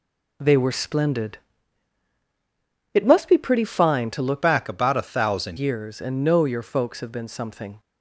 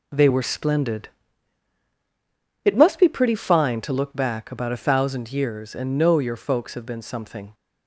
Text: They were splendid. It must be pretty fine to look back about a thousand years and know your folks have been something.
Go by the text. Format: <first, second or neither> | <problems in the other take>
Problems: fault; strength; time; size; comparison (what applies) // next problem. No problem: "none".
second | changes voice from "back" to "thousand"; from 4.4 to 5.5 s; 1.1 s long